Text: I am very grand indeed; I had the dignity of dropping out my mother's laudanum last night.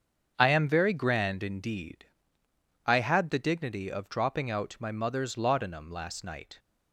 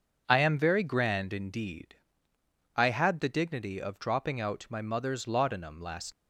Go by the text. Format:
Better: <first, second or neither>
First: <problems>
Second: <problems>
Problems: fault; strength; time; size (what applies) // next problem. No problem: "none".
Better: first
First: starts louder than the rest; until 1.3 s; 7 dB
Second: starts louder than the rest; until 1.2 s; 6.5 dB // stops before "night"; at 6.1 s